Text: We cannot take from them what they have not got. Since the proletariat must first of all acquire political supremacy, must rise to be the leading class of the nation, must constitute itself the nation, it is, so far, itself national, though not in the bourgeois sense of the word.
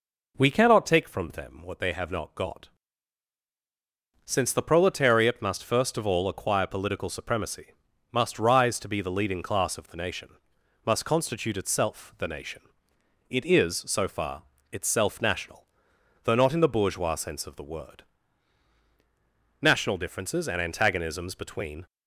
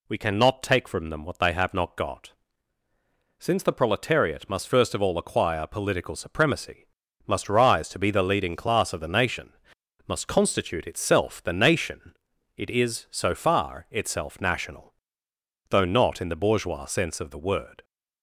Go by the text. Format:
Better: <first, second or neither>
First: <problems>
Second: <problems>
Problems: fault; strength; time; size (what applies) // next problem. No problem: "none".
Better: second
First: goes on to say "National differences and antagonisms between"; strong; from 19.6 s on; 2.2 s long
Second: none